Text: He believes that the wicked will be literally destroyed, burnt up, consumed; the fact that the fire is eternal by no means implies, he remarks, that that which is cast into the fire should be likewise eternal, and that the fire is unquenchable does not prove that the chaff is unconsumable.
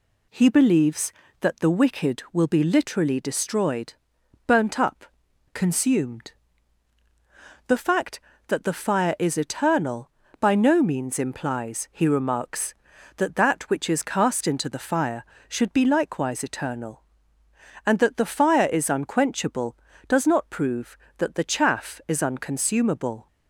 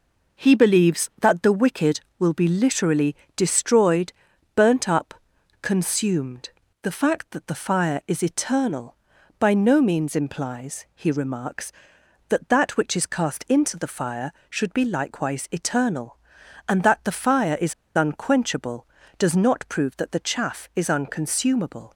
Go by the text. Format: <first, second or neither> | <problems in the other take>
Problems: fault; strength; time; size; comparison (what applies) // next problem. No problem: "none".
first | pauses between "literally" and "destroyed"; slight; at 3.1 s; 0.20 s long // pauses between "is" and "unquenchable"; slight; at 17.7 s; 0.22 s long